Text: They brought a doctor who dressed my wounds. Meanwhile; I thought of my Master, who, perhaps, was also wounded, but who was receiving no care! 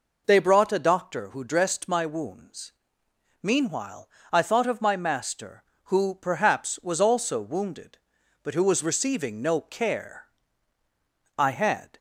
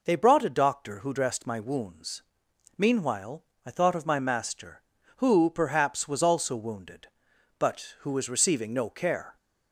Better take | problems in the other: second | goes on to say "I had"; from 11.3 s on; 0.60 s long

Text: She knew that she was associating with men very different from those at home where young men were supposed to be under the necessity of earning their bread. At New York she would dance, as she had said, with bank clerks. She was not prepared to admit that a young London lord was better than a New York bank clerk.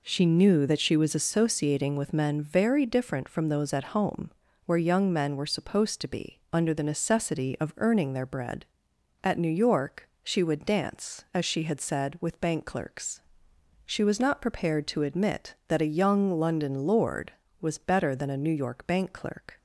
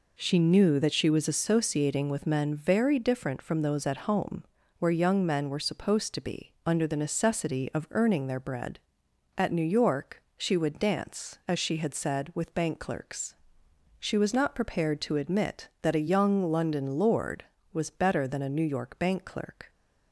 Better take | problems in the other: neither | pauses between "home" and "where"; slight; the same in both // pauses between "York" and "she"; slight; the same in both

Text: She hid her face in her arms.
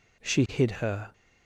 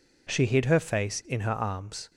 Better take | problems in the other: second | stops before "face in her arms"; at 1.1 s

